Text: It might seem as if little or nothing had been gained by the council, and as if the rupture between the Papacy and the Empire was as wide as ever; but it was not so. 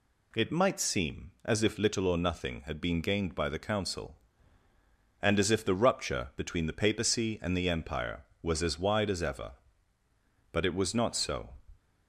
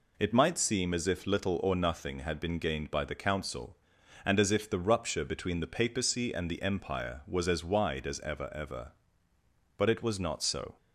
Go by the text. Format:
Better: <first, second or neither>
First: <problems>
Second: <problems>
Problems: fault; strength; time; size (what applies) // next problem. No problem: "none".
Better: first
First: none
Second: says "ever" twice; at 8.5 s